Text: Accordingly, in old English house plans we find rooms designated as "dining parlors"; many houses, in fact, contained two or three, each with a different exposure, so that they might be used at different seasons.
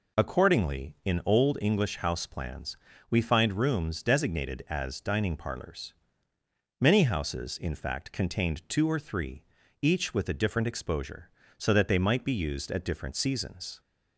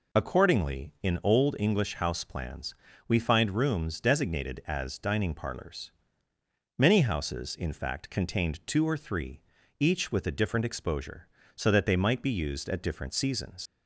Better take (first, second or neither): first